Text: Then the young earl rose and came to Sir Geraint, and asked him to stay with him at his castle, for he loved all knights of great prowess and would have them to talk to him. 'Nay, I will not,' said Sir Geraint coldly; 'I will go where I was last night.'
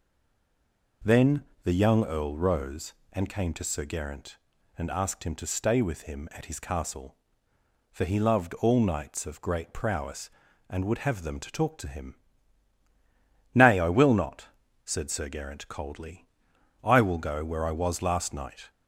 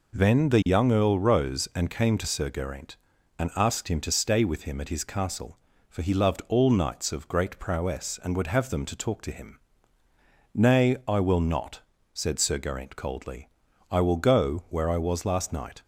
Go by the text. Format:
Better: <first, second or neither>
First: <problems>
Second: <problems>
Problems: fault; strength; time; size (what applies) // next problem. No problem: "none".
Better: second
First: stays silent before the first word; until 1.0 s; 1.0 s long // pauses between "Then" and "the"; slight; at 1.4 s; 0.22 s long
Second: none